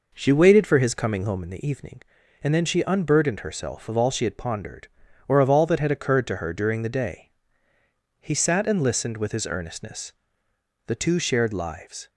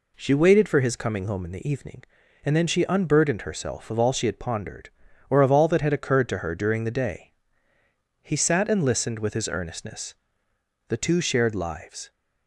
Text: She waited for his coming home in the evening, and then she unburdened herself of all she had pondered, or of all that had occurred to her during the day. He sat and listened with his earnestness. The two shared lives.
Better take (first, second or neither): second